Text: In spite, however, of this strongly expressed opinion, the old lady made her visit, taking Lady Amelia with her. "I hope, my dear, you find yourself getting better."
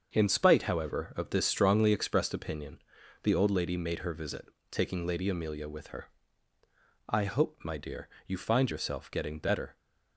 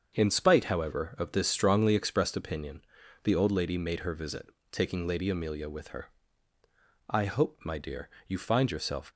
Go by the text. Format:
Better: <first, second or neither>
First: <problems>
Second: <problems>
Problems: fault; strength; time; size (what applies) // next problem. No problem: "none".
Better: first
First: starts louder than the rest; until 1.1 s; 6.5 dB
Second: starts louder than the rest; until 1.1 s; 6.5 dB // stops before "getting better"; at 9.1 s